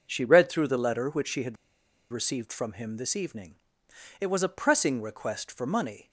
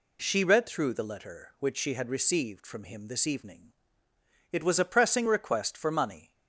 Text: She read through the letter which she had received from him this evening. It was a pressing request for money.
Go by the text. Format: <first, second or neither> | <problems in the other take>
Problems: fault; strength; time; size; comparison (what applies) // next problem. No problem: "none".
second | pauses between "had" and "received"; noticeable; at 1.5 s; 0.57 s long